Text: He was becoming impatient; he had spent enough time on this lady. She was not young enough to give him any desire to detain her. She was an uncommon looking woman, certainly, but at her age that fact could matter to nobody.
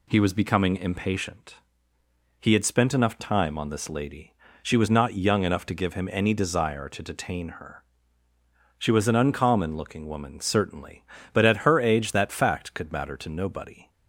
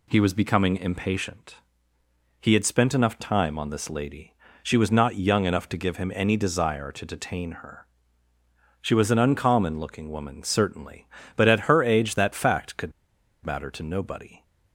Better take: first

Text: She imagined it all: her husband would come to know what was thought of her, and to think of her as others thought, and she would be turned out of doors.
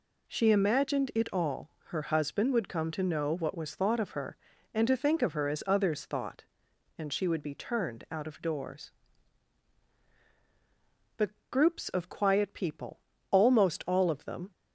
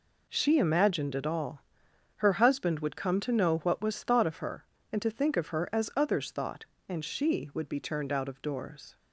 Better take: second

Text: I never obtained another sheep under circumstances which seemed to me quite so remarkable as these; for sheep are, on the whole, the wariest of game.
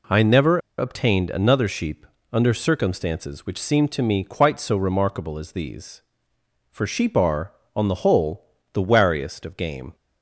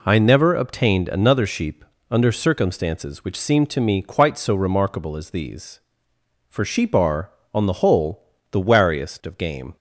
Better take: second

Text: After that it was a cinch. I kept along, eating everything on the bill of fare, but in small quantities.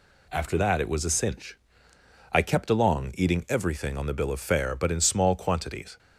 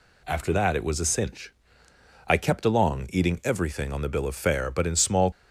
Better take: first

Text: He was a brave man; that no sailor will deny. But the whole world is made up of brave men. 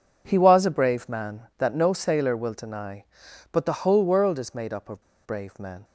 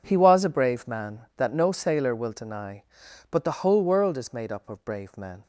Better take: second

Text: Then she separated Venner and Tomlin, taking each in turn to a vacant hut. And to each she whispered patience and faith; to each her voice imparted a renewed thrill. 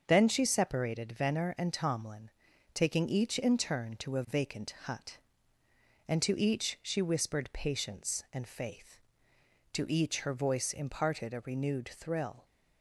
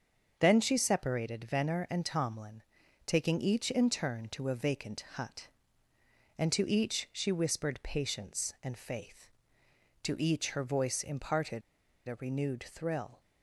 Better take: first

